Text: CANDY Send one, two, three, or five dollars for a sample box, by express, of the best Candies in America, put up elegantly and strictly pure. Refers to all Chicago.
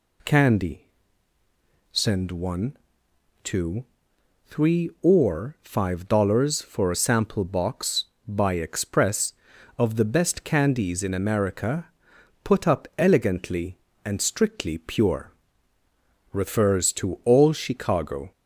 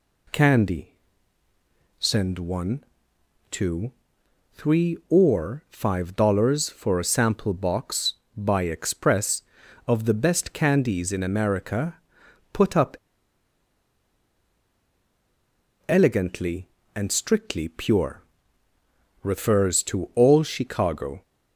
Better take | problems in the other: first | pauses between "CANDY" and "Send"; at 0.9 s; 1.0 s long; also in the first // pauses between "up" and "elegantly"; strong; at 12.9 s; 2.9 s long

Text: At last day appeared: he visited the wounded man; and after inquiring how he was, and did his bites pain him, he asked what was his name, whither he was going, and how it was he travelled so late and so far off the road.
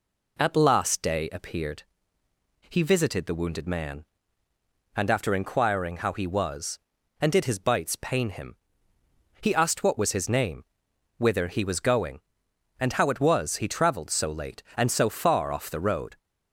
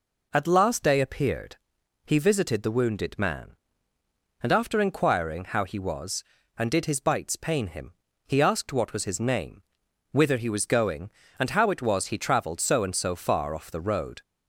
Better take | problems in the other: first | skips "late"; at 12.8 s

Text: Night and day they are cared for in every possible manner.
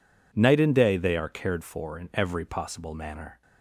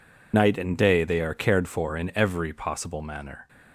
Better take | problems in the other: first | loses the start of "Night"; at 0.3 s; 55 ms

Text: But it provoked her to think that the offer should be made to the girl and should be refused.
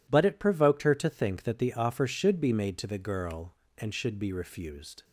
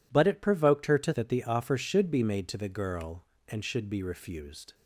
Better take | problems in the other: first | skips "think"; at 1.1 s

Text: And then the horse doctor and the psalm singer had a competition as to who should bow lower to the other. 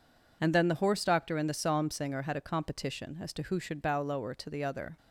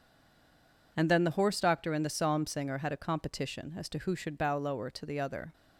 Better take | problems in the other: first | stays silent before the first word; slight; until 0.9 s; 0.9 s long

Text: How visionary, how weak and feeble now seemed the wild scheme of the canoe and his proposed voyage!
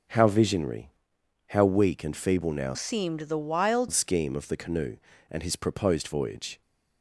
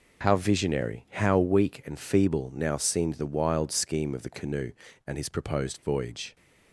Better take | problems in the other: second | starts louder than the rest; until 1.7 s; 6.5 dB // changes voice from "seemed" to "wild"; from 2.7 to 3.8 s; 1.1 s long

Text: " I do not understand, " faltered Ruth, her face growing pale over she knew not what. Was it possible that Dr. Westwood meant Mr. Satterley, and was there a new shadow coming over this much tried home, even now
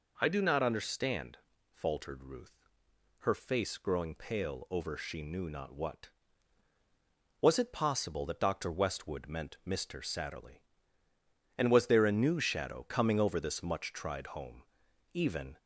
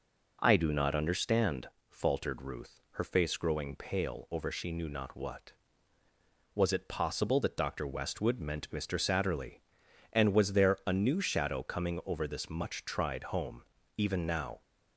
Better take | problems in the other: second | stops before "now"; at 15.5 s

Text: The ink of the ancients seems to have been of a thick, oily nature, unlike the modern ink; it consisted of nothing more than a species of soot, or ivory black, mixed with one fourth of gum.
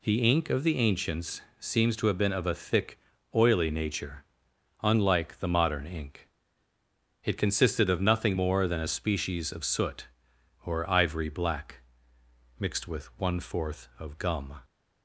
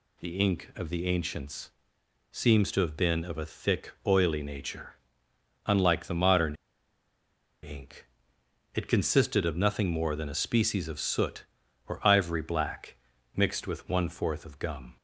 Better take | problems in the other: first | pauses between "ancients" and "seems"; noticeable; at 1.7 s; 0.60 s long; slight in the first // pauses between "modern" and "ink"; at 6.5 s; 1.0 s long

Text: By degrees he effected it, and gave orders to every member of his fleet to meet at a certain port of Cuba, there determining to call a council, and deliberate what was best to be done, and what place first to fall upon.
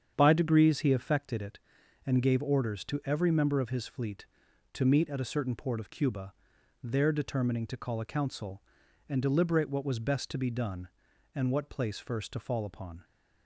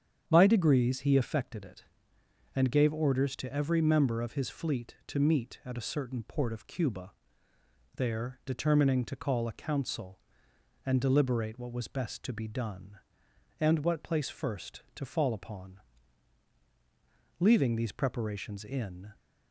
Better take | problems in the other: first | starts louder than the rest; strong; until 1.2 s; 8 dB; strong in the first // goes on to say "Leaving these preparations in"; strong; from 17.4 s on; 1.7 s long

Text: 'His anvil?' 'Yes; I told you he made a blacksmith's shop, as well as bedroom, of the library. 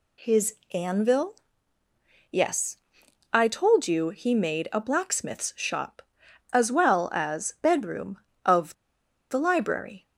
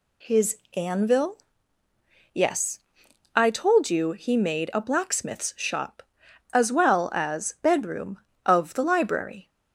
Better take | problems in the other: second | pauses between "His" and "anvil"; slight; at 0.5 s; 0.18 s long; slight in the second // pauses between "of" and "the"; noticeable; at 8.7 s; 0.57 s long

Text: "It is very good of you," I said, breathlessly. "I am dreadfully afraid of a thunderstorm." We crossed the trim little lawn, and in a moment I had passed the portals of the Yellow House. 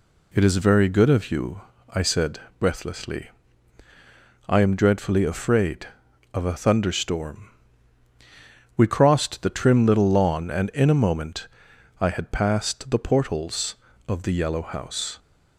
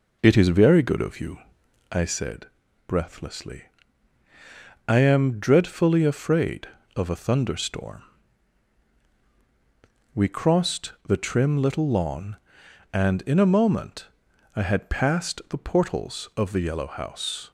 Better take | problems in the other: first | starts louder than the rest; noticeable; until 2.1 s; 4 dB // pauses between "moment" and "I"; noticeable; at 14.0 s; 0.48 s long; noticeable in the first

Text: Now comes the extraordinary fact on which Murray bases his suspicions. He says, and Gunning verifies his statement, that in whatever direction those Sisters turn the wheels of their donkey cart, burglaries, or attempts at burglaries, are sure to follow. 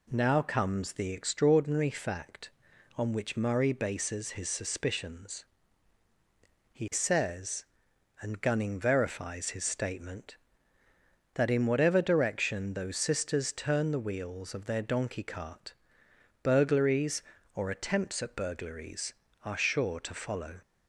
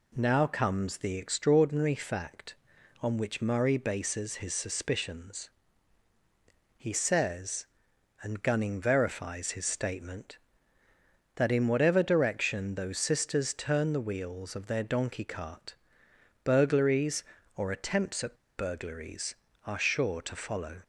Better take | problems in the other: first | pauses between "at" and "burglaries"; slight; at 18.3 s; 0.20 s long

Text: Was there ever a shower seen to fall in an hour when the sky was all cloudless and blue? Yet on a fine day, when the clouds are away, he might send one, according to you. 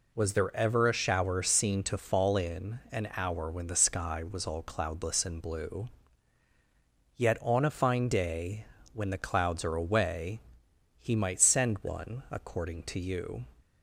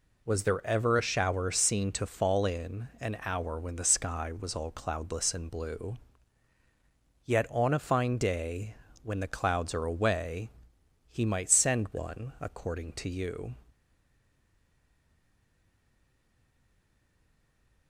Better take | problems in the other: first | stays silent after the last word; strong; from 13.7 s on; 4.1 s long

